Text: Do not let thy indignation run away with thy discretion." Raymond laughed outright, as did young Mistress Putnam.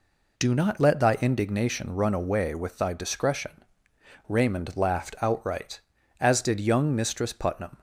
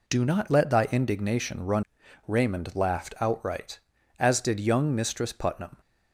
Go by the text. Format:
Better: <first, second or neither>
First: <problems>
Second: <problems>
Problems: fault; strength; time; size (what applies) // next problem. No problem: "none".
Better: first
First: none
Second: skips "away with thy discretion"; at 2.0 s